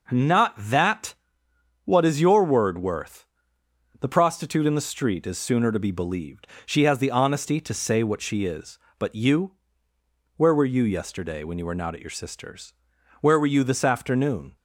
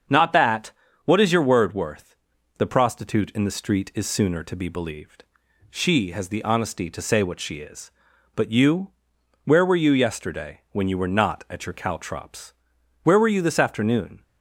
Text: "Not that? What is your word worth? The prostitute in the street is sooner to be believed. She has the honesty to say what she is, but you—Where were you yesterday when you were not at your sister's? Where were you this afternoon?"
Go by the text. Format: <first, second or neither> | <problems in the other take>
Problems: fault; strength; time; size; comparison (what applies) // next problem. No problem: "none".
first | starts louder than the rest; until 1.4 s; 7 dB // says "caltrops" for "sister's"; at 11.7 s